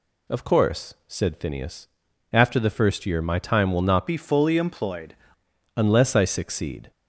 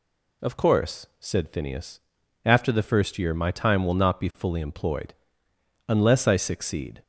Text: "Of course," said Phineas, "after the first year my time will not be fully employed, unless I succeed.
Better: second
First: changes voice from "be" to "employed"; from 4.0 to 5.1 s; 1.1 s long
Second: none

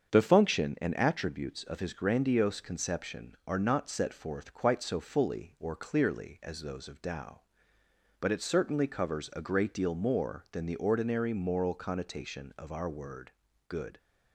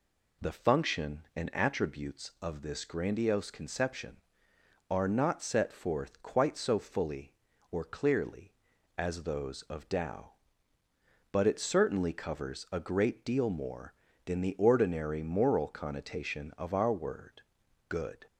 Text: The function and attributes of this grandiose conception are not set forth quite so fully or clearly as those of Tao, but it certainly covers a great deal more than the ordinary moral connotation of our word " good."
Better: second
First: starts louder than the rest; strong; until 1.2 s; 7 dB // says "his" for "this"; at 1.8 s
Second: none

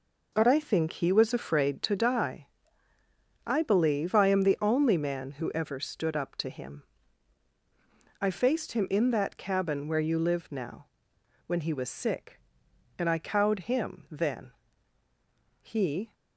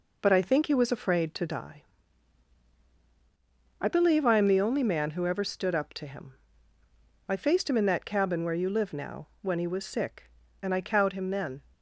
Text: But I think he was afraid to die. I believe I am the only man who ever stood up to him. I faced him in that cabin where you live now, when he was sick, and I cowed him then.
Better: second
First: goes on to say "He"; from 15.6 s on; 0.52 s long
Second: none

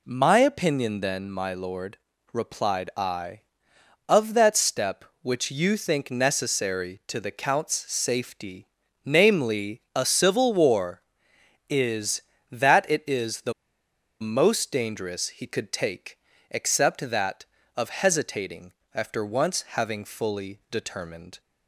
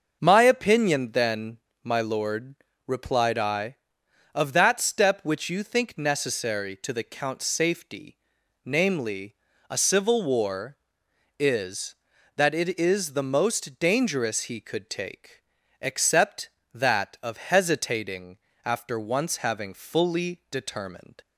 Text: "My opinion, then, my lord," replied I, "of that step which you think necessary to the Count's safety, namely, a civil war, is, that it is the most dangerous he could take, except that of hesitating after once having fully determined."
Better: second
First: pauses between "the" and "most"; noticeable; at 13.5 s; 0.69 s long // pauses between "hesitating" and "after"; slight; at 18.7 s; 0.22 s long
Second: pauses between "hesitating" and "after"; slight; at 18.3 s; 0.26 s long

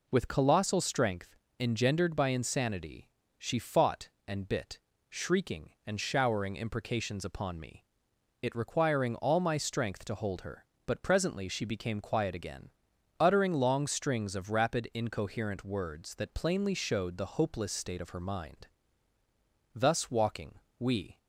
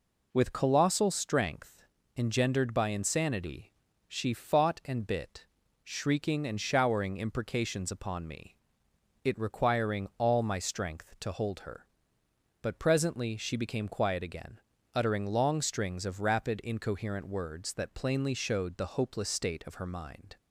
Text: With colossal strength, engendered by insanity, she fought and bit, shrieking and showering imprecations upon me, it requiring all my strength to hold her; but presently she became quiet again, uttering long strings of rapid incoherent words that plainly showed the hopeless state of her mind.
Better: second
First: goes on to say "Thus walking we"; from 19.7 s on; 1.4 s long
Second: none

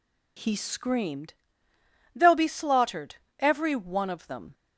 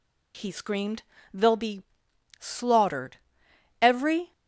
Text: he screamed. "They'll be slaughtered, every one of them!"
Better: first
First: none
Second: pauses between "be" and "slaughtered"; noticeable; at 1.8 s; 0.56 s long // stops before "one of them"; at 4.3 s

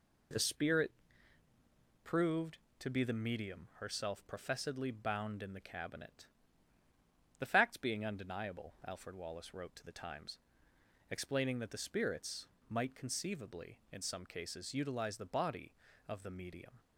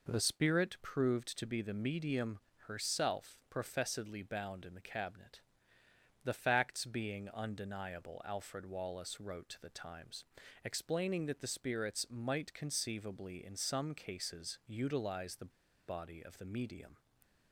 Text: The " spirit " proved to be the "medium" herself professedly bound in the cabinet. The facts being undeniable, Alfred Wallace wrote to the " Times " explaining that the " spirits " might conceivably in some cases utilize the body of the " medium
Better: first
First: none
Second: pauses between "medium" and "herself"; slight; at 2.3 s; 0.28 s long // pauses between "the" and "body"; at 15.5 s; 0.37 s long

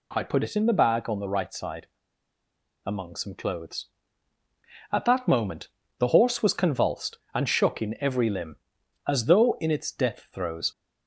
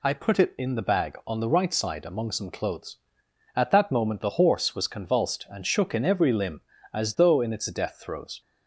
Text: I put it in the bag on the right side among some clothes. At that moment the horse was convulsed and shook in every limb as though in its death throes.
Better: second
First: pauses between "side" and "among"; at 1.8 s; 0.99 s long // pauses between "moment" and "the"; slight; at 5.6 s; 0.28 s long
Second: none

